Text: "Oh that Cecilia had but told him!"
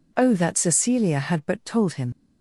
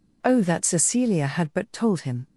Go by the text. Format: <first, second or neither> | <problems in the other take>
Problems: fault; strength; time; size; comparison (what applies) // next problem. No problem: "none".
second | leaves "him" unfinished; at 2.1 s; 65 ms